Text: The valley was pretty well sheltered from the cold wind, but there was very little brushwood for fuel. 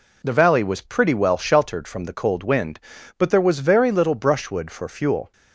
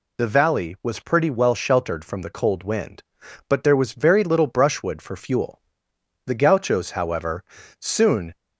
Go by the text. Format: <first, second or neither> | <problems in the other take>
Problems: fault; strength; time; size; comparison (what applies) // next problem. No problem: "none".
first | goes on to say "The Gauchos however soon"; strong; from 6.2 s on; 2.0 s long